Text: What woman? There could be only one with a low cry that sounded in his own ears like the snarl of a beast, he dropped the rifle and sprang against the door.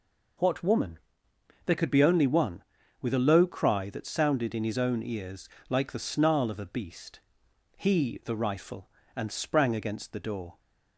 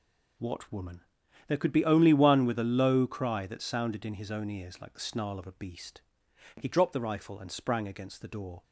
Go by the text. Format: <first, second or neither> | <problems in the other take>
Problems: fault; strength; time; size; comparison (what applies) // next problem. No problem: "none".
second | pauses between "ears" and "like"; slight; at 5.4 s; 0.20 s long // skips "dropped"; at 8.2 s